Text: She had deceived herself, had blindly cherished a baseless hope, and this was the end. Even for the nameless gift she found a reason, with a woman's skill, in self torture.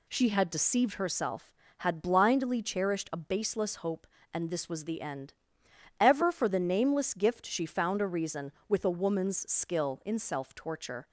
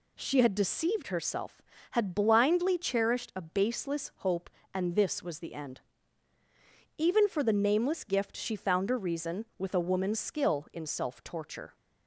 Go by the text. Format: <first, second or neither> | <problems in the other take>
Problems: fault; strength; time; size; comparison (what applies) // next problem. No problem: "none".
second | says "Ever" for "Even"; at 6.0 s